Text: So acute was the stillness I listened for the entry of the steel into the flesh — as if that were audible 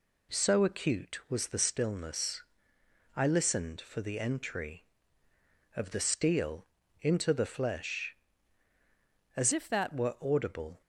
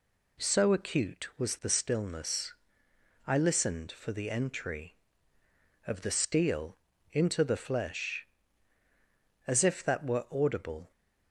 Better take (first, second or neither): second